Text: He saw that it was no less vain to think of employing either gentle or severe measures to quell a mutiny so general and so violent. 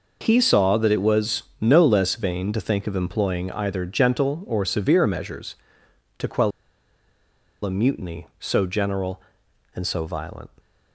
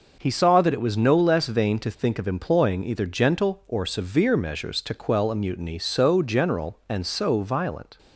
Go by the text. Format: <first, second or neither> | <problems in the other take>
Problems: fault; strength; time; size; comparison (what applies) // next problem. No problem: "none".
second | pauses between "was" and "no"; slight; at 1.4 s; 0.18 s long // pauses between "quell" and "a"; at 6.5 s; 1.1 s long